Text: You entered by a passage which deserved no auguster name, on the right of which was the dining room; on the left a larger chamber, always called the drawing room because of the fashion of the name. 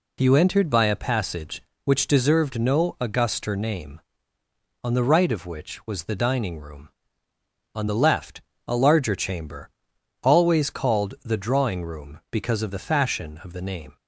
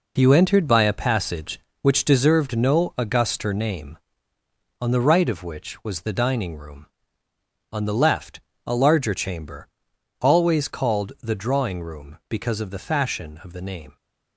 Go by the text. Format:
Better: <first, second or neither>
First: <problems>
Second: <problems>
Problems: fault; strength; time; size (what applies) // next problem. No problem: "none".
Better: first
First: pauses between "left" and "a"; slight; at 8.4 s; 0.24 s long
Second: gets quieter; strong; throughout; 8 dB // pauses between "left" and "a"; slight; at 8.4 s; 0.24 s long